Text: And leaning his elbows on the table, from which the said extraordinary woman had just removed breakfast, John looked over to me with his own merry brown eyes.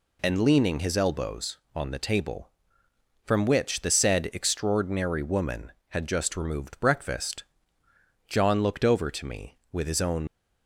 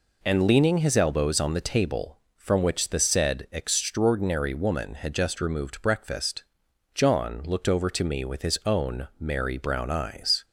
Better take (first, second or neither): second